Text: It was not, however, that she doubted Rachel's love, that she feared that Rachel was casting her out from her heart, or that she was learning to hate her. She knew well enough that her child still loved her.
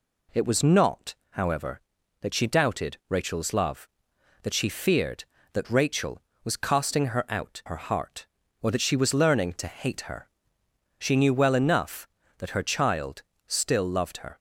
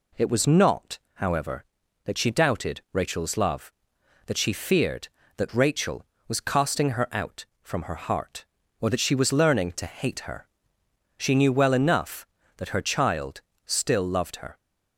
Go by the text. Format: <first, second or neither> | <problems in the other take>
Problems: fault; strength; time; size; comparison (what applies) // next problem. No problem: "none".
second | skips "from"; at 7.6 s // pauses between "child" and "still"; slight; at 13.2 s; 0.24 s long; slight in the second